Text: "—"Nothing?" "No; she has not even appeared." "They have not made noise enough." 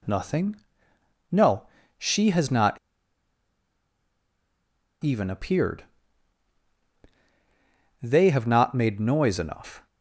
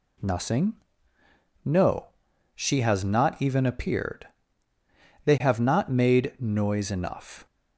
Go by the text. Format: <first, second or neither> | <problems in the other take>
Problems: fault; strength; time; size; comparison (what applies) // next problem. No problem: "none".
second | pauses between "not" and "even"; strong; at 2.7 s; 2.2 s long